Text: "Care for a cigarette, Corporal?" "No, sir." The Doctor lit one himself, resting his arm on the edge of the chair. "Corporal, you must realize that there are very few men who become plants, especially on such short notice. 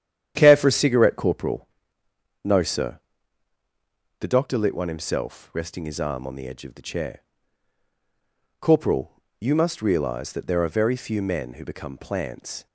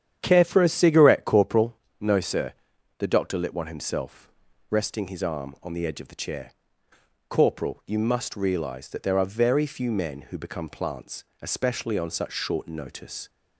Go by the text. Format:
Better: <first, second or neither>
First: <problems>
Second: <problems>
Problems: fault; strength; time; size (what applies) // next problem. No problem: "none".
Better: second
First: starts louder than the rest; strong; until 1.3 s; 10 dB // stops before "especially on such short notice"; at 12.6 s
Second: starts louder than the rest; strong; until 1.2 s; 9 dB